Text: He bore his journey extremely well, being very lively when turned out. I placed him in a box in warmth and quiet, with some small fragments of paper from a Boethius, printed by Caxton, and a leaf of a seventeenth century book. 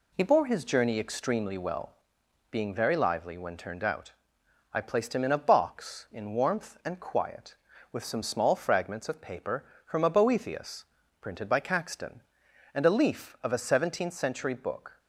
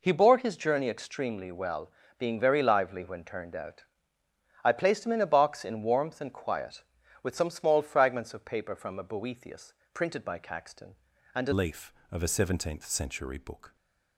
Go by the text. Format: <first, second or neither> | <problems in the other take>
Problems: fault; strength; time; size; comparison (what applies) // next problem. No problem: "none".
first | changes voice at "leaf"; from 11.5 s on; 2.2 s long